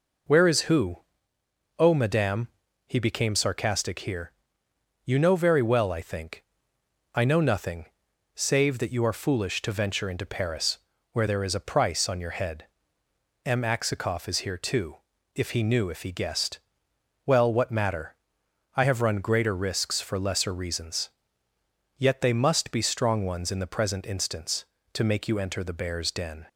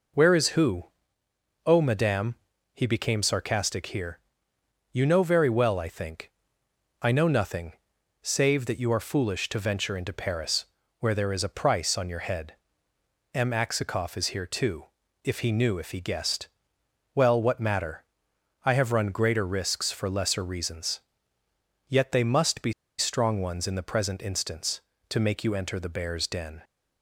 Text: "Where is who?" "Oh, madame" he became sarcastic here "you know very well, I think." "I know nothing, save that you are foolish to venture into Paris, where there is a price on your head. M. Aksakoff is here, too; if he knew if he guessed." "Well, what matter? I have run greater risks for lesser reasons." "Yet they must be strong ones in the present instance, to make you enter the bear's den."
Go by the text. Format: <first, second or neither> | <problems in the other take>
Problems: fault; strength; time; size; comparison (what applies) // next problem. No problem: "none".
first | pauses between "madame" and "he"; slight; at 2.3 s; 0.36 s long; slight in the first // pauses between "here" and "you"; noticeable; at 4.2 s; 0.72 s long; noticeable in the first // pauses between "be" and "strong"; slight; at 22.7 s; 0.27 s long